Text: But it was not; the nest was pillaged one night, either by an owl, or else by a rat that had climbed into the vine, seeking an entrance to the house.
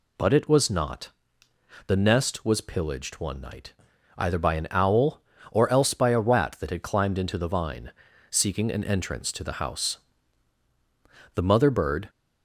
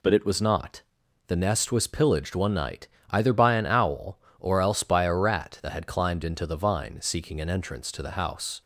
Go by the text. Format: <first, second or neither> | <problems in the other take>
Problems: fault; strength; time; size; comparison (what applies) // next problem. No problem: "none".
second | goes on to say "The mother bird"; noticeable; from 11.3 s on; 0.76 s long